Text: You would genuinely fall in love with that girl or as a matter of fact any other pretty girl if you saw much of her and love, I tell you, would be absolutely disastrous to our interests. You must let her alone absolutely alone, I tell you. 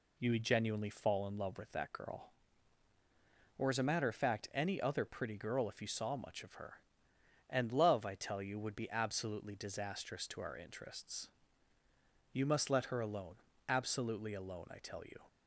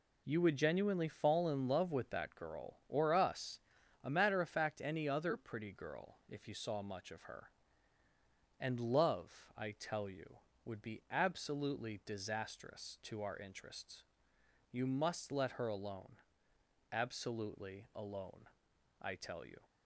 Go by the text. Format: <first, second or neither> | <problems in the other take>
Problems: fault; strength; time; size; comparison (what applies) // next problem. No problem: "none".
first | says "us" for "as"; at 3.1 s // pauses between "alone" and "absolutely"; noticeable; at 16.1 s; 0.74 s long; slight in the first